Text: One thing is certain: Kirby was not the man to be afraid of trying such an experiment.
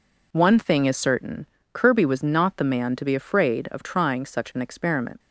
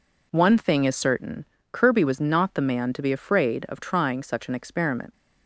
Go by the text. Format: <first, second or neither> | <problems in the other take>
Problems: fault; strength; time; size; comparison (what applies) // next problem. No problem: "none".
neither | none